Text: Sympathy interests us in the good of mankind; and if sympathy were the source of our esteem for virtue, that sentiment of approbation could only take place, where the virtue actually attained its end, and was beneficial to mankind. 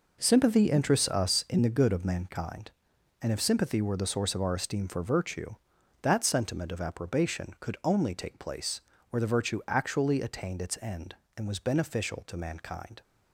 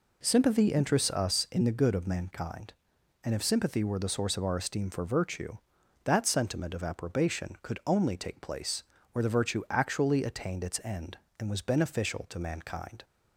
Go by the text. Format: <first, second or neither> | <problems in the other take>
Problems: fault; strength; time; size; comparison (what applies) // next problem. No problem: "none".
second | gets quieter; strong; throughout; 9.5 dB